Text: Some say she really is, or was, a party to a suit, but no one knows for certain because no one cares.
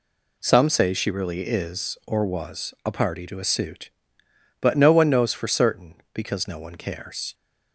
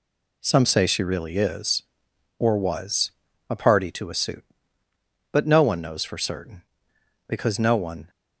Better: first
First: none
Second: stops before "cares"; at 8.0 s

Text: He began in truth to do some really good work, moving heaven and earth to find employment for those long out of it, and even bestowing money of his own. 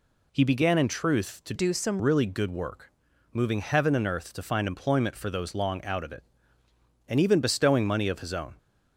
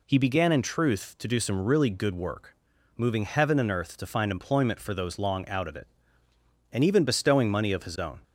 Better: second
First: changes voice from "do" to "some"; from 1.5 to 2.0 s; 0.5 s long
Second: none

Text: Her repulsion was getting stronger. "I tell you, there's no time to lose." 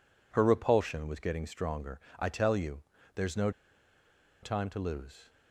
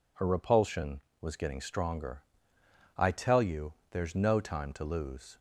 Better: second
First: pauses between "no" and "time"; noticeable; at 3.4 s; 0.92 s long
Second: none

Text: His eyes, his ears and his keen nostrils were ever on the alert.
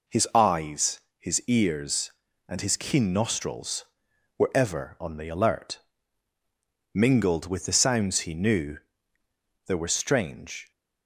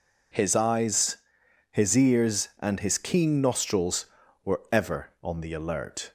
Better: second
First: goes on to say "Mingled with the sounds he knew there were strange"; strong; from 6.9 s on; 3.7 s long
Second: none

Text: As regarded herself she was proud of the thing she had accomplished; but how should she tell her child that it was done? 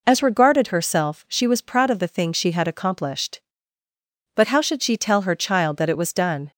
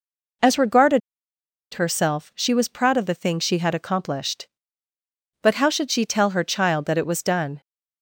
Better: first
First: none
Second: pauses between "regarded" and "herself"; noticeable; at 1.0 s; 0.74 s long

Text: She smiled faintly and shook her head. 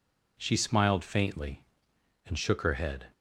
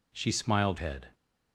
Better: first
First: none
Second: skips "faintly and shook her"; at 0.7 s

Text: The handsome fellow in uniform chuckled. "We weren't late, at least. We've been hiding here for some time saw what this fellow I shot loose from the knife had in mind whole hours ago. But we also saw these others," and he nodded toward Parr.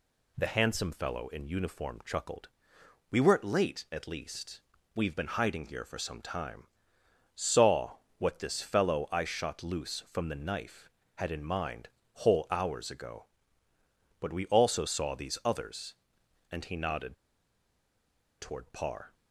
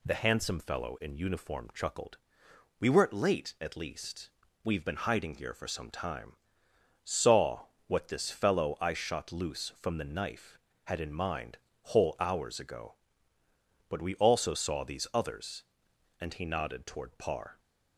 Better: second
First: pauses between "time" and "saw"; noticeable; at 6.6 s; 0.66 s long // pauses between "saw" and "what"; slight; at 7.9 s; 0.18 s long // pauses between "mind" and "whole"; slight; at 11.8 s; 0.26 s long // pauses between "nodded" and "toward"; strong; at 17.1 s; 1.2 s long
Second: pauses between "time" and "saw"; noticeable; at 6.3 s; 0.66 s long // pauses between "saw" and "what"; slight; at 7.6 s; 0.18 s long // pauses between "mind" and "whole"; slight; at 11.5 s; 0.26 s long

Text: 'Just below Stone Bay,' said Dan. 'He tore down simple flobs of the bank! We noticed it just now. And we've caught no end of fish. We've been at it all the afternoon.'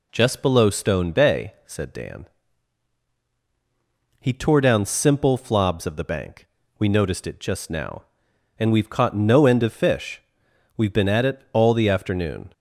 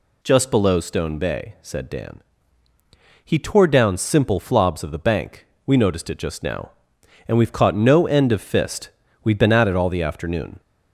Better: first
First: none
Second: says "fist" for "fish"; at 8.4 s

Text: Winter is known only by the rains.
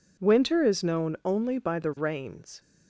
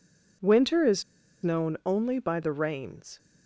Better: first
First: none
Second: pauses between "is" and "known"; at 1.0 s; 0.40 s long

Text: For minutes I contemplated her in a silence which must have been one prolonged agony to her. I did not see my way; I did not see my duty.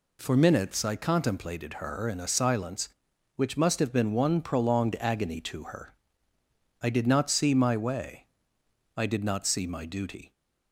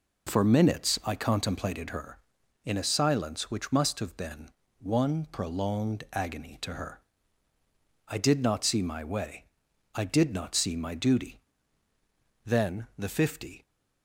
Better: first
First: none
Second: pauses between "been" and "one"; slight; at 4.4 s; 0.28 s long // goes on to say "Then the fifty"; noticeable; from 12.4 s on; 1.1 s long

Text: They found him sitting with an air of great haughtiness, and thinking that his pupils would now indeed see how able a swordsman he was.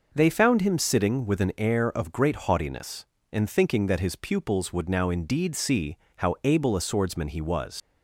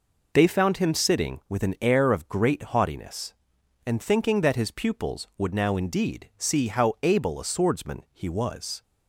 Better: second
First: pauses between "see" and "how"; slight; at 5.9 s; 0.20 s long // leaves "was" unfinished; at 7.8 s; 85 ms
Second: none

